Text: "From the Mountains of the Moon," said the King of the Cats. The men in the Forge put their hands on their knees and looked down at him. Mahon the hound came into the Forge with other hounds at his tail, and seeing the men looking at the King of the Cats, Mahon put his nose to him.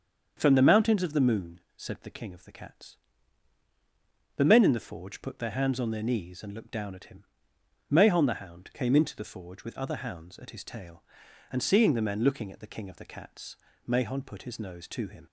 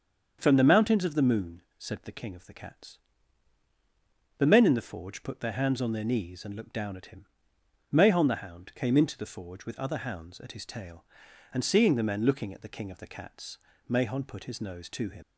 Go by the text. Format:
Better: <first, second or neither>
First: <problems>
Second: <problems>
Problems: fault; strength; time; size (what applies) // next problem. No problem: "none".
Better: first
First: starts louder than the rest; until 1.3 s; 7 dB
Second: starts louder than the rest; until 1.4 s; 7 dB // leaves "him" unfinished; at 15.2 s; 45 ms